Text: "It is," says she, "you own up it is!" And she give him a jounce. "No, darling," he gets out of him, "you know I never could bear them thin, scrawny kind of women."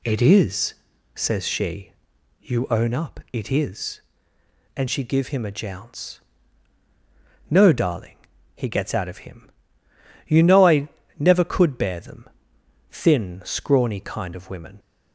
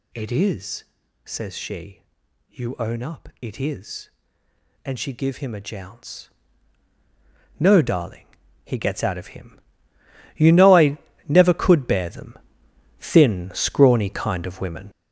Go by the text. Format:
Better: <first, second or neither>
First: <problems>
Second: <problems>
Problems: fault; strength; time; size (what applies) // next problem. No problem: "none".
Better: first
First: pauses between "I" and "never"; slight; at 10.8 s; 0.32 s long // pauses between "them" and "thin"; noticeable; at 12.2 s; 0.62 s long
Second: gets louder; strong; throughout; 8 dB // pauses between "I" and "never"; slight; at 10.9 s; 0.32 s long // pauses between "them" and "thin"; noticeable; at 12.3 s; 0.62 s long